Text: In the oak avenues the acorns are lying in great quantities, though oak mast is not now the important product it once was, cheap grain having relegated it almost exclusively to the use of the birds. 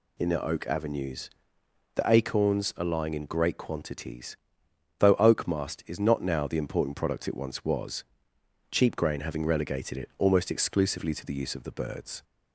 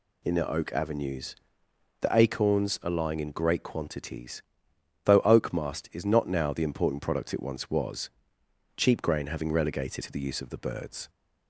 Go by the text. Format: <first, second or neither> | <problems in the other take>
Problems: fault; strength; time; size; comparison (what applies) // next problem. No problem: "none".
first | pauses between "avenues" and "the"; noticeable; at 1.3 s; 0.64 s long; noticeable in the first // skips "it almost exclusively"; at 10.0 s